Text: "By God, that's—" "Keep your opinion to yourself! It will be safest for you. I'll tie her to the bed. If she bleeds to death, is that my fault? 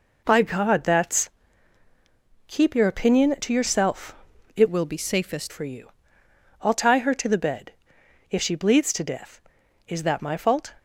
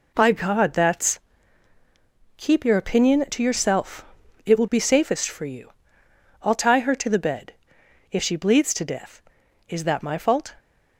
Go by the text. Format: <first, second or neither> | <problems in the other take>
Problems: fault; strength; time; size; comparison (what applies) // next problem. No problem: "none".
second | changes voice from "will" to "safest"; from 4.6 to 5.5 s; 0.9 s long